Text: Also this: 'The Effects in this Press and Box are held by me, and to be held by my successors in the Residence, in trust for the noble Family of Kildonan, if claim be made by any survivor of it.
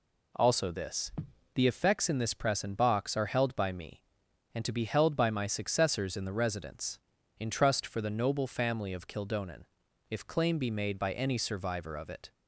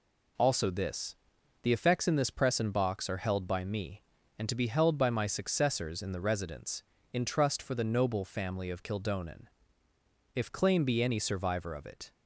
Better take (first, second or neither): first